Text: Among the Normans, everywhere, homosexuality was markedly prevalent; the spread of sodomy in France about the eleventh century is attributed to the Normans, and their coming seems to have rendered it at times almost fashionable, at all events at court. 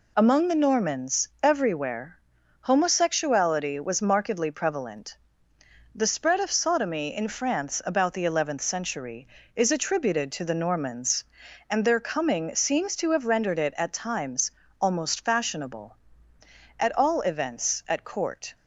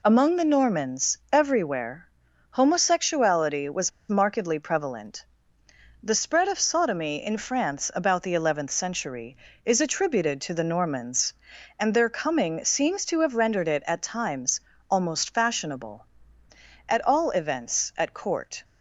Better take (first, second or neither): first